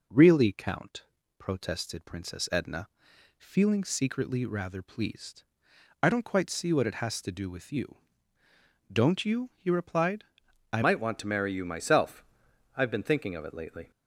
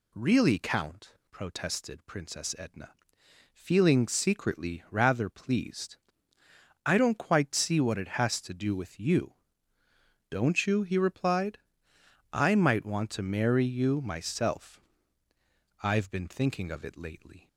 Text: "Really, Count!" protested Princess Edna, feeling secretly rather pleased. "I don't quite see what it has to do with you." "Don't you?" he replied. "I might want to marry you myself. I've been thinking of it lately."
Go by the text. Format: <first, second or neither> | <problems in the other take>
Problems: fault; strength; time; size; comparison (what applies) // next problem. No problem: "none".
second | changes voice at "might"; from 10.8 s on; 3.1 s long